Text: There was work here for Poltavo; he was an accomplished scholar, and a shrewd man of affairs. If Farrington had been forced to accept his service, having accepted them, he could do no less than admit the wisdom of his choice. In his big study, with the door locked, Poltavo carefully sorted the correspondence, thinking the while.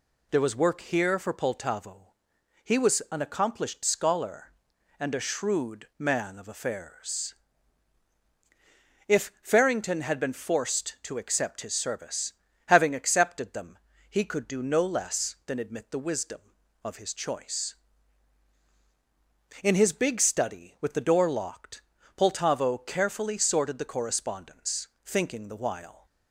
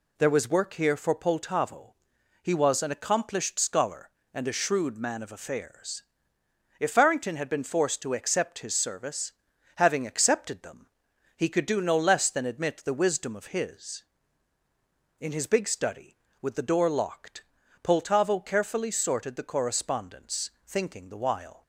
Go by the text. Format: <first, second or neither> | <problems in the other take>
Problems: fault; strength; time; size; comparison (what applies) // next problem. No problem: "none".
first | skips "choice"; at 14.6 s